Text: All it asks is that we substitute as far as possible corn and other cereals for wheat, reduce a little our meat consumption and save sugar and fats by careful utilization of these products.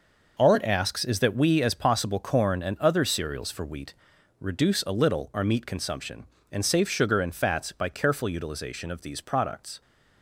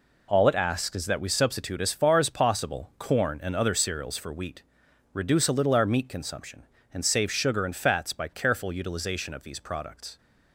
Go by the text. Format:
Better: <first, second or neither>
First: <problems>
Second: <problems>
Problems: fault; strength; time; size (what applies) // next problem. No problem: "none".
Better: second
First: skips "substitute as far"; at 1.6 s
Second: none